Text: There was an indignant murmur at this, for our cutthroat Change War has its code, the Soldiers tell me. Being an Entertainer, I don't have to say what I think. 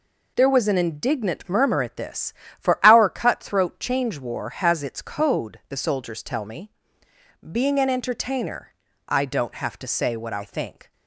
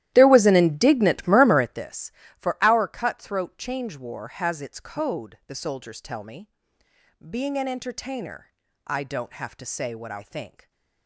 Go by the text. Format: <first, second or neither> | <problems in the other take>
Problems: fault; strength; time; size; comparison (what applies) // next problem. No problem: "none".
first | starts louder than the rest; strong; until 1.9 s; 14 dB